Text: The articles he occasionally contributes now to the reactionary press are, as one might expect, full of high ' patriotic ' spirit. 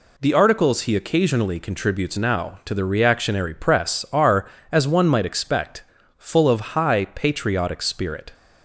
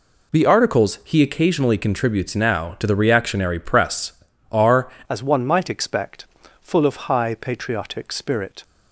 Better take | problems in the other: first | changes voice at "as"; from 5.0 s on; 3.6 s long

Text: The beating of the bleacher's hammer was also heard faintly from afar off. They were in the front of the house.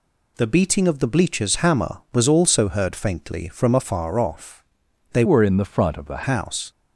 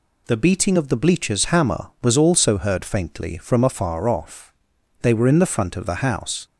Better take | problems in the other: second | changes voice from "were" to "the"; from 5.2 to 6.2 s; 1.0 s long

